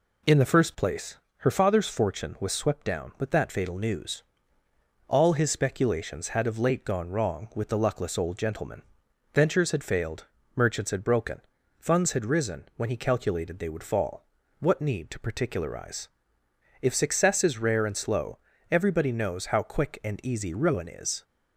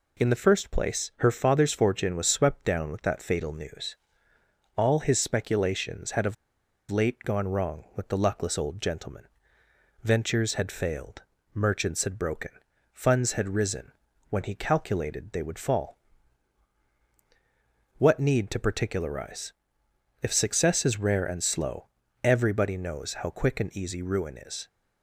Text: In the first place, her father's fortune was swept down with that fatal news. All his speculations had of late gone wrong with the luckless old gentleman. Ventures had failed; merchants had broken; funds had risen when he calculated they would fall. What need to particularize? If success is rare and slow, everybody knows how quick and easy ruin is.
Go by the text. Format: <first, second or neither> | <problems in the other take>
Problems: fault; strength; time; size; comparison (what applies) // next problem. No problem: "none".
first | pauses between "of" and "late"; noticeable; at 6.3 s; 0.56 s long // pauses between "risen" and "when"; at 13.9 s; 0.38 s long